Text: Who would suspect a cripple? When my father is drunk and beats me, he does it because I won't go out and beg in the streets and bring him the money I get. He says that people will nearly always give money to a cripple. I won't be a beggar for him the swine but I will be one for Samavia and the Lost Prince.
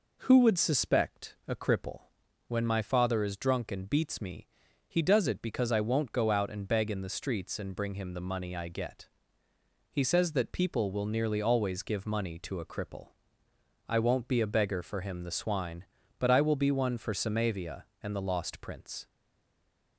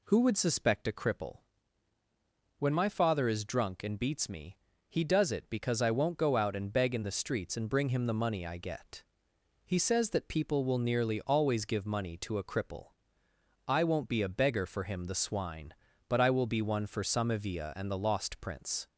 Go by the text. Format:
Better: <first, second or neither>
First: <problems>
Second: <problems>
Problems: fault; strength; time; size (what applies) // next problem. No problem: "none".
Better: second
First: stays silent after the last word; slight; from 19.0 s on; 0.9 s long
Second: none